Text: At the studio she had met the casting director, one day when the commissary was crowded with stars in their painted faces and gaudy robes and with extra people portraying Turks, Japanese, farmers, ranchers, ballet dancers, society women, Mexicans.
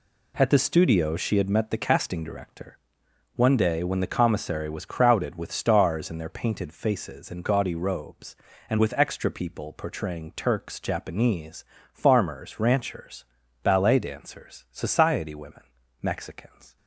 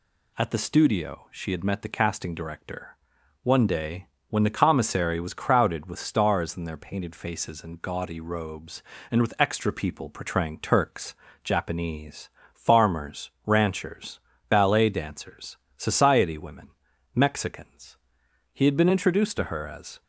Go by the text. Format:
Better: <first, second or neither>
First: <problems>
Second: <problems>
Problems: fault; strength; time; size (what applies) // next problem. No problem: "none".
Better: first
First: none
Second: pauses between "day" and "when"; slight; at 4.0 s; 0.22 s long // goes on to say "He had been introduced to her as"; from 18.5 s on; 1.5 s long